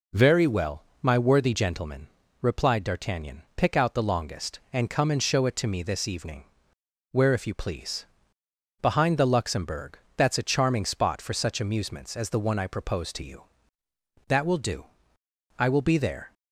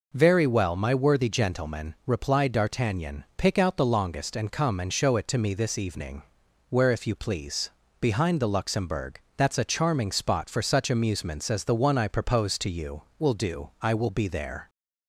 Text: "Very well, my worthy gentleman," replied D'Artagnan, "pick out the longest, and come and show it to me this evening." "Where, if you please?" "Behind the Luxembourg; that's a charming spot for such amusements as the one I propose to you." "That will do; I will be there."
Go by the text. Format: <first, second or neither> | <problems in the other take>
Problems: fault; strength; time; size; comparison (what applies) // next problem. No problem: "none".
first | skips "That"; at 13.1 s